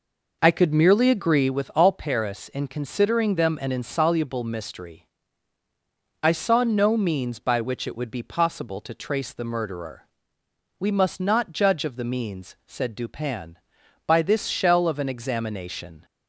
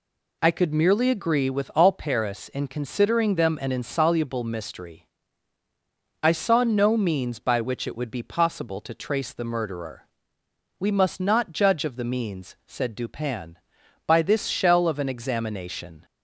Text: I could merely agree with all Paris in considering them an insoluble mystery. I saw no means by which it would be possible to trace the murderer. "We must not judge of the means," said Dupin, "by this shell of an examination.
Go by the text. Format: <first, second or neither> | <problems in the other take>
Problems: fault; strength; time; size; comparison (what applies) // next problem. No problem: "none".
second | starts louder than the rest; noticeable; until 1.7 s; 5 dB